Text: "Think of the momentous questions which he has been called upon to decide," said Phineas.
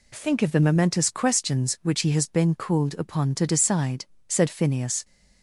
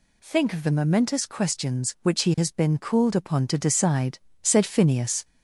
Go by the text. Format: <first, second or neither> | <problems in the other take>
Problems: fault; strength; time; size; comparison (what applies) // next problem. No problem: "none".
first | gets louder; slight; throughout; 2.5 dB